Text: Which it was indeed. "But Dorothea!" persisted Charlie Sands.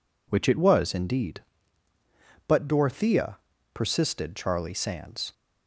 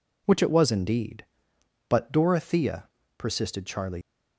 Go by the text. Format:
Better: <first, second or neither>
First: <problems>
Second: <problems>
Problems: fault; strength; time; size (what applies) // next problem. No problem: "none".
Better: first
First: none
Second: stops before "Sands"; at 4.0 s